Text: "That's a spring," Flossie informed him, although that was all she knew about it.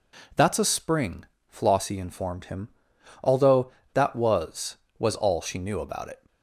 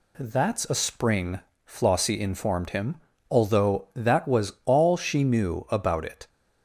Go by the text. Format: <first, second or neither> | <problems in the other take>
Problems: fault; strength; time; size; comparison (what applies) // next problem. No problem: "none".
second | says "was" twice; at 4.9 s